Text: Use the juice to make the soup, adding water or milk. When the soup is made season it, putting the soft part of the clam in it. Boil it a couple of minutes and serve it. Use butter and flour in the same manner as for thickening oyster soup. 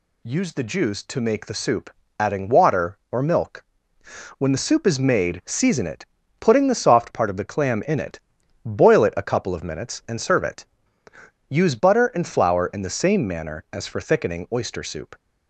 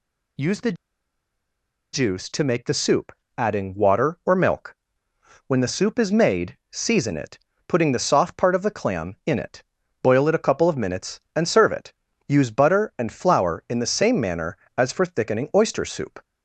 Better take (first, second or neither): first